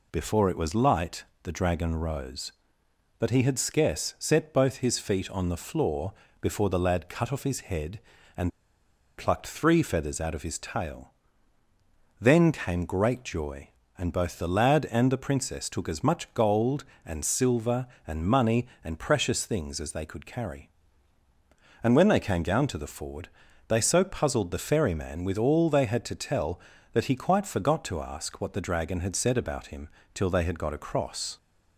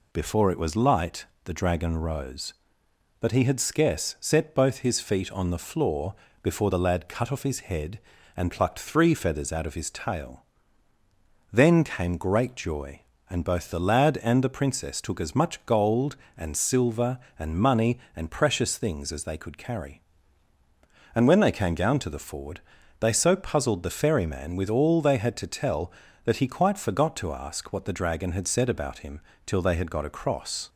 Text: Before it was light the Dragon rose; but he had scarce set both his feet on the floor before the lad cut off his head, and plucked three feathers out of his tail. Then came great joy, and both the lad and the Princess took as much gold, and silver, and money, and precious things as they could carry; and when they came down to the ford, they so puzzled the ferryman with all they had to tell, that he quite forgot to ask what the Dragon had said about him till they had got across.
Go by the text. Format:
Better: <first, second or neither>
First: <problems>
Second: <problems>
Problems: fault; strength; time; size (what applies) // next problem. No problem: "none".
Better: second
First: pauses between "light" and "the"; slight; at 1.2 s; 0.20 s long // pauses between "floor" and "before"; slight; at 6.1 s; 0.26 s long // pauses between "and" and "plucked"; noticeable; at 8.4 s; 0.67 s long // pauses between "him" and "till"; slight; at 29.8 s; 0.28 s long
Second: pauses between "light" and "the"; slight; at 1.2 s; 0.20 s long // pauses between "floor" and "before"; slight; at 6.1 s; 0.26 s long // pauses between "him" and "till"; slight; at 29.1 s; 0.28 s long